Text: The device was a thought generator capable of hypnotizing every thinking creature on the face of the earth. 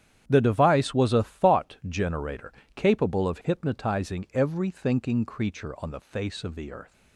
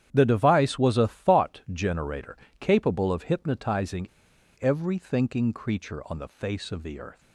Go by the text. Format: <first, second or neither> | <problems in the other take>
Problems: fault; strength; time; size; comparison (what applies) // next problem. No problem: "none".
first | starts louder than the rest; strong; until 1.1 s; 10 dB; strong in the first // pauses between "generator" and "capable"; slight; at 2.3 s; 0.22 s long; slight in the first // pauses between "hypnotizing" and "every"; noticeable; at 4.0 s; 0.53 s long